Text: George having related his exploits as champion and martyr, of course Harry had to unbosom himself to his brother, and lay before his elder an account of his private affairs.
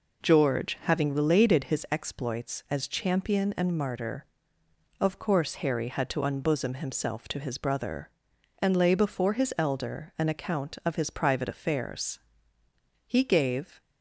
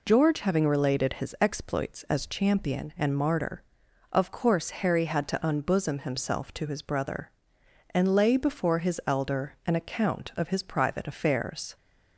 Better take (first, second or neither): second